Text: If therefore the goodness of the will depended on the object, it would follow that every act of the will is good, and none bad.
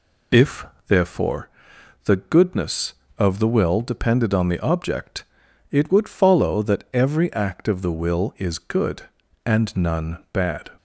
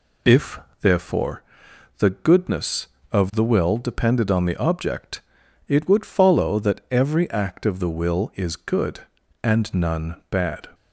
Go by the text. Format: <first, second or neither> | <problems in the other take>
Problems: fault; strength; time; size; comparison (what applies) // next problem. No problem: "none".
neither | pauses between "If" and "therefore"; slight; the same in both // pauses between "therefore" and "the"; noticeable; the same in both